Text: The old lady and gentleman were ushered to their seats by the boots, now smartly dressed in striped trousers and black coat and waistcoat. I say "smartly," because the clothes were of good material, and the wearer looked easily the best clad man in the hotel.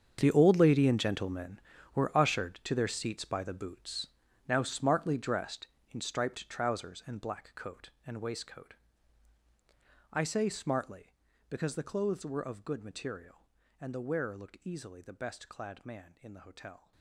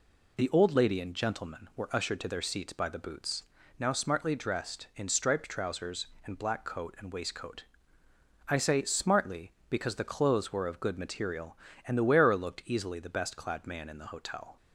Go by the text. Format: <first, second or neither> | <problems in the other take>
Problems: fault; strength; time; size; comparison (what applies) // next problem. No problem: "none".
second | gets quieter; strong; throughout; 16 dB